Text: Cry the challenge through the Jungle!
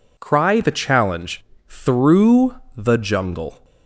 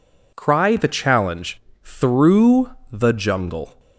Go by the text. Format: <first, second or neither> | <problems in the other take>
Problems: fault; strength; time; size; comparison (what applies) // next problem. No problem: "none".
neither | pauses between "challenge" and "through"; slight; the same in both // pauses between "through" and "the"; slight; the same in both